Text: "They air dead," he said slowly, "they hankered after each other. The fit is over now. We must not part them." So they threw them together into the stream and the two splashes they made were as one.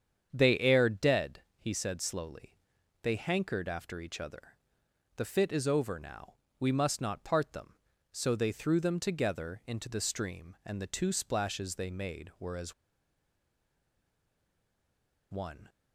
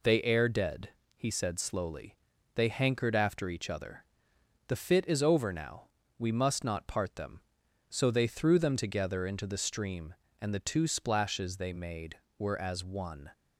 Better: second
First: starts louder than the rest; strong; until 1.3 s; 7.5 dB // pauses between "as" and "one"; strong; at 12.7 s; 2.5 s long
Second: none

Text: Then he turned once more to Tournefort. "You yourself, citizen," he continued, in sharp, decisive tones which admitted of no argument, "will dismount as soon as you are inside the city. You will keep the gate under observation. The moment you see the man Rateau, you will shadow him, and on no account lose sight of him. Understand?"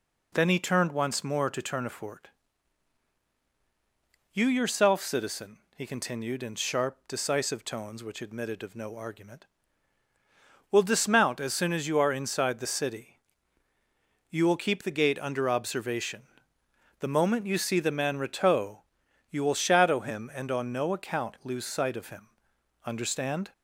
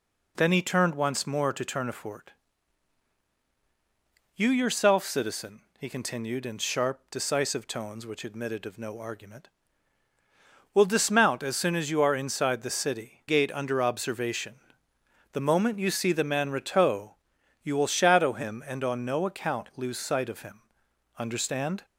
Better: first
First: none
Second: skips "You will keep the"; at 13.2 s

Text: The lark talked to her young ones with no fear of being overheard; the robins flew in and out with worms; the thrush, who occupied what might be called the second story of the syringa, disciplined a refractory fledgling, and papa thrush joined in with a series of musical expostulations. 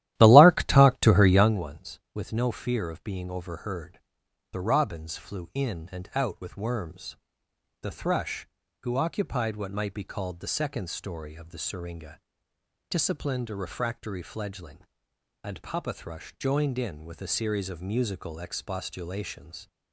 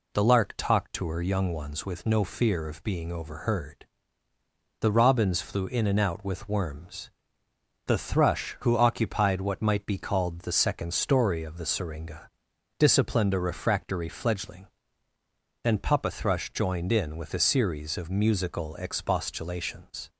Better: second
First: starts louder than the rest; strong; until 1.6 s; 13.5 dB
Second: none

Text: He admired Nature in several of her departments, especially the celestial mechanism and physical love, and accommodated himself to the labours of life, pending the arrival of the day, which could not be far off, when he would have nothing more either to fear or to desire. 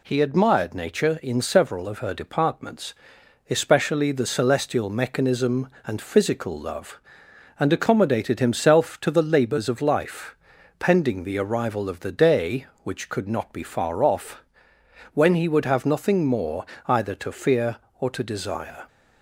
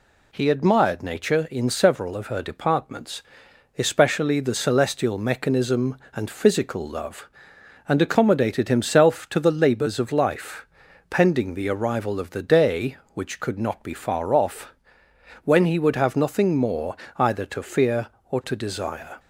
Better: neither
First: pauses between "more" and "either"; slight; at 16.6 s; 0.22 s long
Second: pauses between "more" and "either"; slight; at 16.9 s; 0.22 s long

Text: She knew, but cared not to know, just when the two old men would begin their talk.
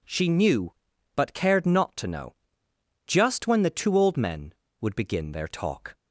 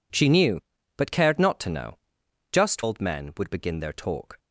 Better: first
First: none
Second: skips "when the two"; at 2.8 s

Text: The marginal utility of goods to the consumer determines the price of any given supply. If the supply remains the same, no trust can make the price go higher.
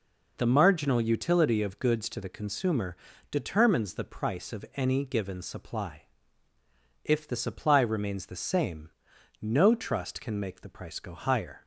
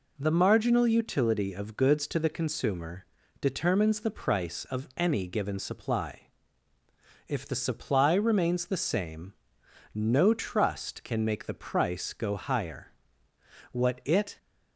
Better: first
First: pauses between "consumer" and "determines"; slight; at 2.9 s; 0.34 s long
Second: pauses between "consumer" and "determines"; at 3.0 s; 0.38 s long // goes on to say "What it"; noticeable; from 13.7 s on; 0.64 s long

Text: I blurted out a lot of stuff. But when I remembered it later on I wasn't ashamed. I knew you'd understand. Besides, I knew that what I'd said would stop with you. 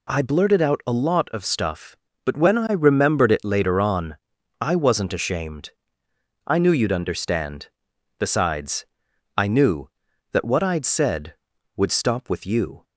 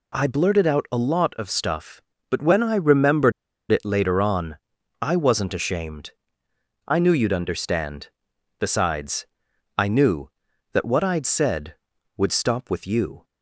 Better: first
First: pauses between "on" and "I"; at 4.1 s; 0.44 s long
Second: pauses between "remembered" and "it"; at 3.3 s; 0.40 s long // pauses between "on" and "I"; at 4.5 s; 0.44 s long

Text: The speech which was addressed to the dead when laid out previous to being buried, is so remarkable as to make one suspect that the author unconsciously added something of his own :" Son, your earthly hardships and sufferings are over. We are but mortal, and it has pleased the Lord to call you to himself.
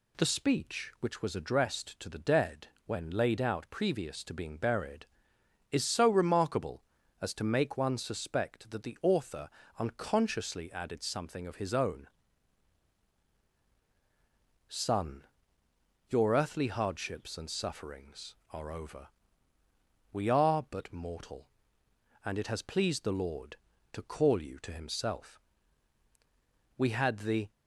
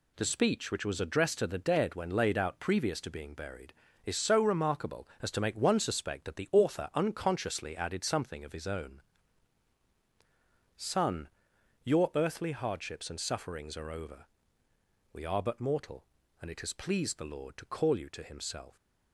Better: second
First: pauses between "dead" and "when"; slight; at 2.6 s; 0.18 s long // pauses between "author" and "unconsciously"; slight; at 9.4 s; 0.30 s long // goes on to say "We had the"; noticeable; from 26.7 s on; 0.72 s long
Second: none

